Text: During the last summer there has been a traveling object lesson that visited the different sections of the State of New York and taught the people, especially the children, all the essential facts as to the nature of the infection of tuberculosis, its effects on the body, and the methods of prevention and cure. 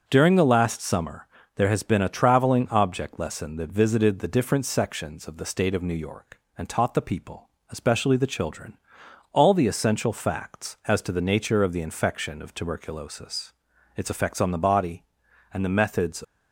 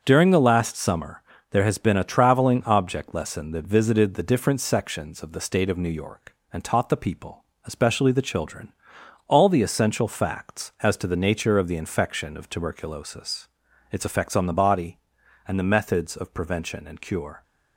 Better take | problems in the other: second | starts louder than the rest; until 1.0 s; 7 dB; also in the second // pauses between "summer" and "there"; slight; at 1.2 s; 0.30 s long; slight in the second // stops before "of prevention and cure"; at 16.2 s

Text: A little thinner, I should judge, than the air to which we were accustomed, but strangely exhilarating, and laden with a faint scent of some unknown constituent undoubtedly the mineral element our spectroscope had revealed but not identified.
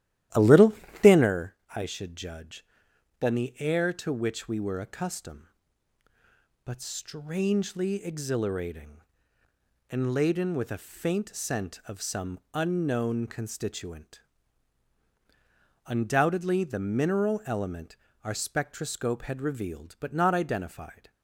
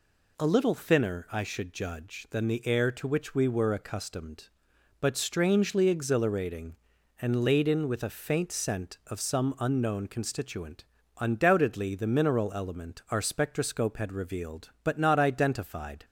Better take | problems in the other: second | starts louder than the rest; strong; until 1.3 s; 13 dB // pauses between "little" and "thinner"; slight; at 0.7 s; 0.30 s long // pauses between "some" and "unknown"; slight; at 12.3 s; 0.16 s long // pauses between "constituent" and "undoubtedly"; strong; at 14.2 s; 1.6 s long; also in the second // pauses between "element" and "our"; slight; at 17.9 s; 0.26 s long

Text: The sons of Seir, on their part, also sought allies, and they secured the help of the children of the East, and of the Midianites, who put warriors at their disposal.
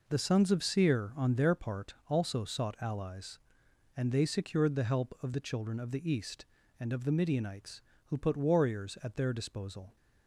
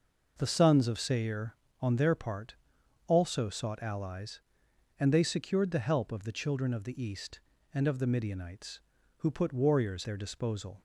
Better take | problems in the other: first | skips "at"; at 10.0 s

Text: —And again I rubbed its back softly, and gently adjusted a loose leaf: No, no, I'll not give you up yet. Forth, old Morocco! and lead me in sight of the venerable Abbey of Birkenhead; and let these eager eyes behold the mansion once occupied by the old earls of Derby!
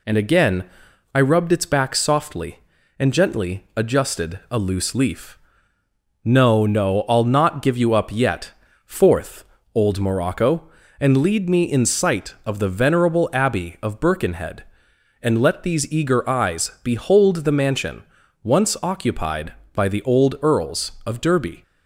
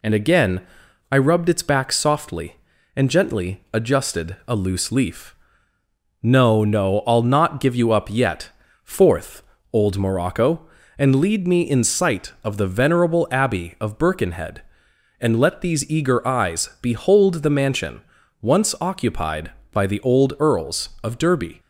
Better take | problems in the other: neither | pauses between "again" and "I"; noticeable; the same in both // pauses between "mansion" and "once"; the same in both

